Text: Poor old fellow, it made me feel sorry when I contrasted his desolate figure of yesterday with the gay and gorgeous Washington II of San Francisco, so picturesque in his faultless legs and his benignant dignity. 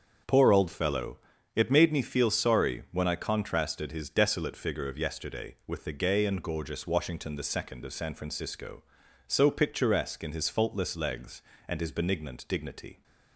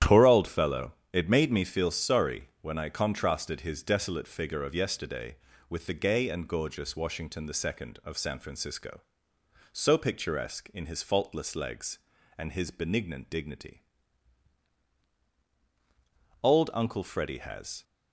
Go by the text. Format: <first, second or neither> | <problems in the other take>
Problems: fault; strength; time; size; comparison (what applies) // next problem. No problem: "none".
first | starts louder than the rest; strong; until 1.2 s; 11 dB; also in the first // goes on to say "Old Uncle Freddy has"; from 16.4 s on; 1.4 s long